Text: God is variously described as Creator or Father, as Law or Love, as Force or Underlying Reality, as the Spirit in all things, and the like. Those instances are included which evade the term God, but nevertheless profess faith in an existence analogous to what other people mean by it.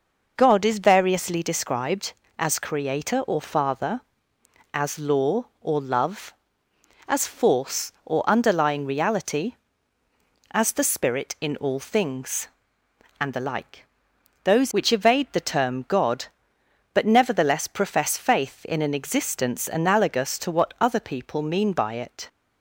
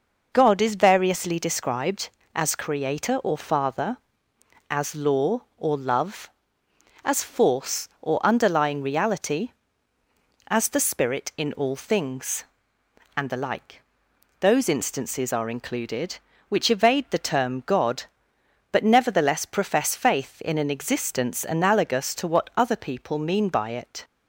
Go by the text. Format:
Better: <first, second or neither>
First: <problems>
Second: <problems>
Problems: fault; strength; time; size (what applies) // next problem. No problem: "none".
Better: second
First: skips "instances are included"; at 14.7 s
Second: none